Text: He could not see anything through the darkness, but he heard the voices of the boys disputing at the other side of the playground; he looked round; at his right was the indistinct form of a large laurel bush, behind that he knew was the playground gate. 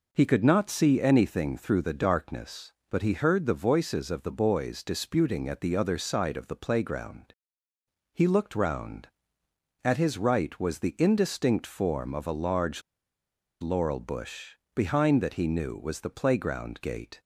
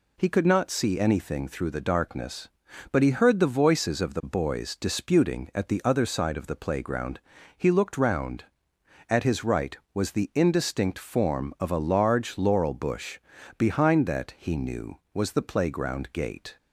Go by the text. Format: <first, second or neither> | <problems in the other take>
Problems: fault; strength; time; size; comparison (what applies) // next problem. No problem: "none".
second | pauses between "large" and "laurel"; noticeable; at 12.8 s; 0.80 s long